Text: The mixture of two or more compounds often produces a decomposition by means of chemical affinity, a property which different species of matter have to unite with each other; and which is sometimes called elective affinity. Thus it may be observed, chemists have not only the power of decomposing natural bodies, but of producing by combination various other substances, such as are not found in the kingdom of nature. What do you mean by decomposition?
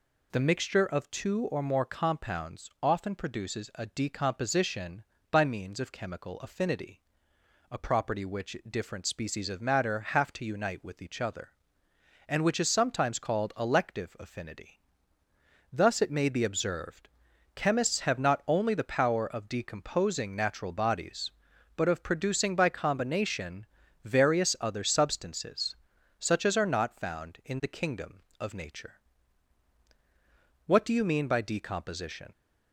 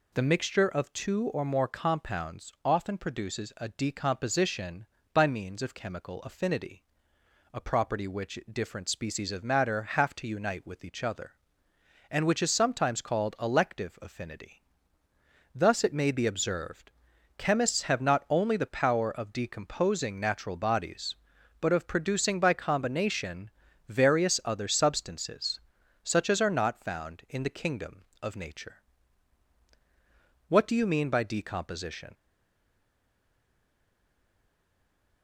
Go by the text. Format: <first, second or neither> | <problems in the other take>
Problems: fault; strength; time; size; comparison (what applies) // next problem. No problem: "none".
first | pauses between "combination" and "various"; at 23.4 s; 0.40 s long; also in the first // stays silent after the last word; strong; from 32.1 s on; 3.1 s long